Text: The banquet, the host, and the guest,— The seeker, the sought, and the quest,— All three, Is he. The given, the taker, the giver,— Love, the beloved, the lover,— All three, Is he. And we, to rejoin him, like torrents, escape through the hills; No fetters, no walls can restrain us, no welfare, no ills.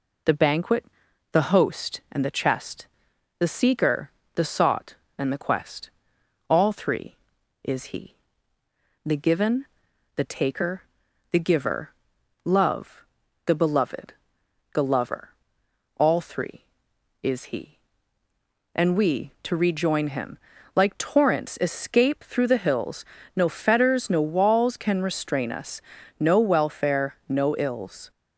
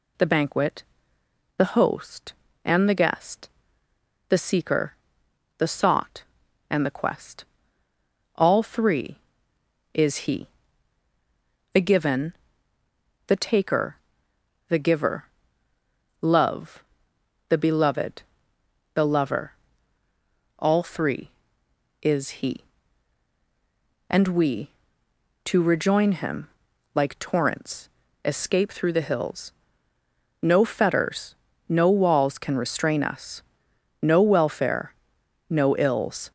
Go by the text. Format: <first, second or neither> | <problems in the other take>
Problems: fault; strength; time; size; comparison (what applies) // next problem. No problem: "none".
second | says "chest" for "guest"; at 2.2 s